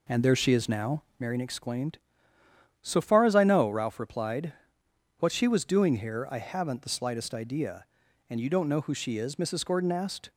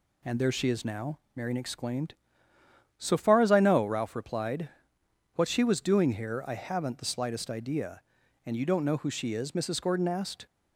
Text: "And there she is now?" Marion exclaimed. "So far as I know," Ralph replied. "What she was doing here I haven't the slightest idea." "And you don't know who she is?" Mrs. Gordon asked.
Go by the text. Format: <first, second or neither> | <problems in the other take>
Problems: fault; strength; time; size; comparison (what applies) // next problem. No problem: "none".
second | starts louder than the rest; slight; until 1.3 s; 3 dB